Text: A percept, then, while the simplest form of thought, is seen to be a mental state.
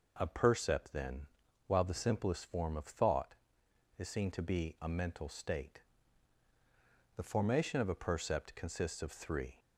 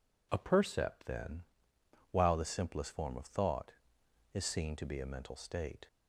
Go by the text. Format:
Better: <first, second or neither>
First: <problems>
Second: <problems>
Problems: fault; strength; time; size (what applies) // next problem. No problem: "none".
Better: second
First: goes on to say "The formation of a percept consists of three"; strong; from 7.1 s on; 2.4 s long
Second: none